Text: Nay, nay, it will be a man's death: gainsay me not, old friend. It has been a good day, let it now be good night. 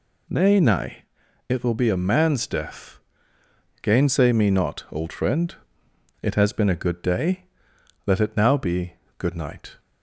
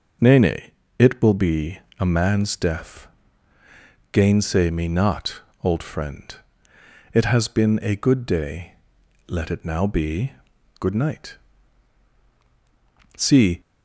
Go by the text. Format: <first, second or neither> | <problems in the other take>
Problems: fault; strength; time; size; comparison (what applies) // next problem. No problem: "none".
first | pauses between "be" and "a"; slight; at 1.7 s; 0.18 s long // pauses between "be" and "good"; noticeable; at 10.3 s; 0.48 s long; slight in the first // goes on to say "See"; slight; from 13.1 s on; 0.44 s long